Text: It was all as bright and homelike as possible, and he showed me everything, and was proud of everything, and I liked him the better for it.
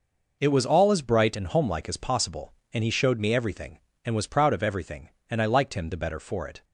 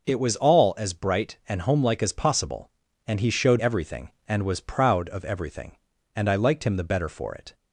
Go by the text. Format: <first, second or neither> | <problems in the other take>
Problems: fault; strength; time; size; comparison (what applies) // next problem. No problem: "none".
first | skips "me"; at 3.5 s